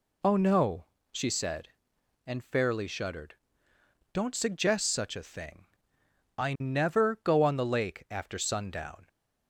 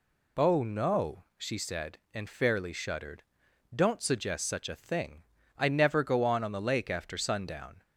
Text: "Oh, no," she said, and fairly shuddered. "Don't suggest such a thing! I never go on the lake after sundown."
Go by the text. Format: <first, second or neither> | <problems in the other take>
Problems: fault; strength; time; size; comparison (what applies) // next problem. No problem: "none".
first | says "on" twice; at 6.4 s